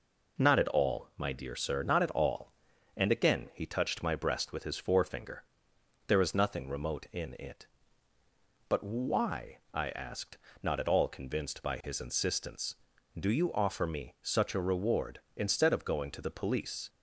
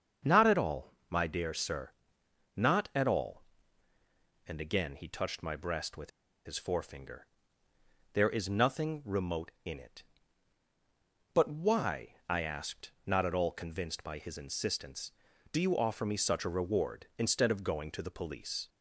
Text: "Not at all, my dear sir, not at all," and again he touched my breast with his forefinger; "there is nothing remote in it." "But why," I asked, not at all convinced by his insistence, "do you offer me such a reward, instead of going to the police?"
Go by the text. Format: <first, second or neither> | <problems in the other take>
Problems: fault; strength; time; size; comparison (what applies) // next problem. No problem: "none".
first | starts louder than the rest; until 1.4 s; 7 dB // pauses between "with" and "his"; at 6.1 s; 0.36 s long